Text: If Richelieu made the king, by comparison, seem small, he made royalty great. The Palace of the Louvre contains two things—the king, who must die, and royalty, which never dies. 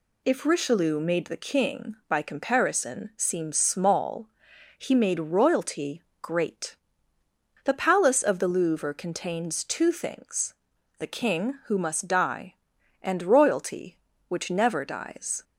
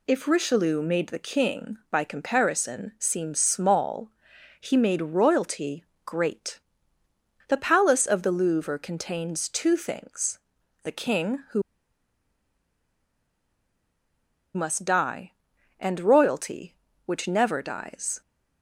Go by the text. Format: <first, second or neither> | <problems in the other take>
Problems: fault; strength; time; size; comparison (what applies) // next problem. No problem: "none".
first | pauses between "royalty" and "great"; slight; at 5.8 s; 0.20 s long; slight in the first // pauses between "who" and "must"; strong; at 11.6 s; 2.9 s long